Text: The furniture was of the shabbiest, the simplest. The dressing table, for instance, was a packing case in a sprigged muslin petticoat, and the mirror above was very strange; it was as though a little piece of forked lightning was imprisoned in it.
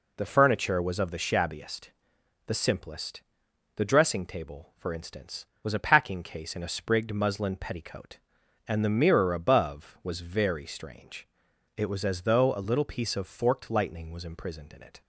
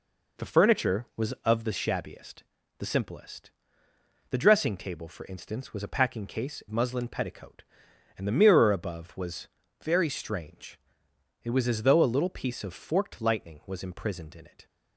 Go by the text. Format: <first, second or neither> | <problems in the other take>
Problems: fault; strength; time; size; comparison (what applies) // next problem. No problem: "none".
first | skips "in a sprigged"; at 6.6 s // pauses between "was" and "very"; slight; at 9.4 s; 0.36 s long